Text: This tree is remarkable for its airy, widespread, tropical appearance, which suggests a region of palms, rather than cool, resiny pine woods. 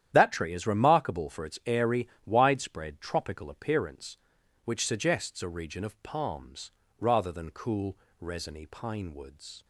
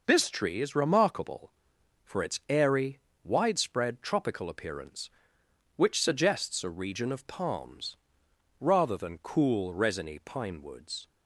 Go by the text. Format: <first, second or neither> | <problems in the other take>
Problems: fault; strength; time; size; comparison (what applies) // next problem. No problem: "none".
second | starts louder than the rest; strong; until 1.1 s; 10.5 dB // says "That" for "This"; at 0.1 s